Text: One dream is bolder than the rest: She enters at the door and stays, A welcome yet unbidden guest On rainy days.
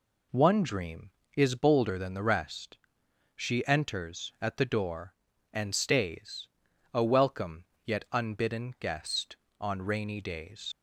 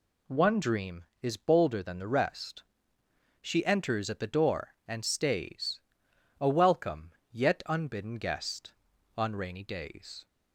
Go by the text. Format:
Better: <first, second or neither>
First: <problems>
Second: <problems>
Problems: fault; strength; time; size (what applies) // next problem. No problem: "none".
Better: second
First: pauses between "welcome" and "yet"; slight; at 7.6 s; 0.22 s long // leaves "days" unfinished; at 10.7 s; 75 ms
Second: pauses between "welcome" and "yet"; slight; at 7.1 s; 0.18 s long